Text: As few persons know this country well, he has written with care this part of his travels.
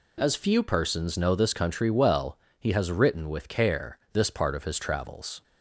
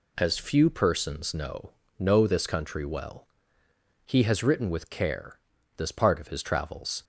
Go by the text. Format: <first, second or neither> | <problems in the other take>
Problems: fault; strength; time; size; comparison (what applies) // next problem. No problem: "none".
first | says "know" twice; at 1.9 s // pauses between "care" and "this"; slight; at 5.3 s; 0.36 s long